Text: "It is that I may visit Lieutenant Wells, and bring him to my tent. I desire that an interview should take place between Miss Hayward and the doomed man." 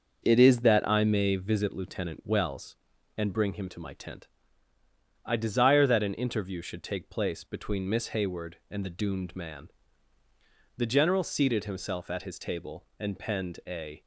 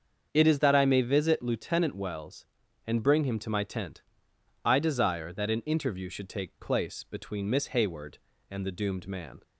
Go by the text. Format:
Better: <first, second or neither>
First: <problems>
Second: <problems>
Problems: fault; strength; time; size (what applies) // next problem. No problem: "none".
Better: second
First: starts louder than the rest; until 1.2 s; 6.5 dB // goes on to say "The General seated himself at his table and penned a"; strong; from 10.7 s on; 3.2 s long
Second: starts louder than the rest; until 1.3 s; 7 dB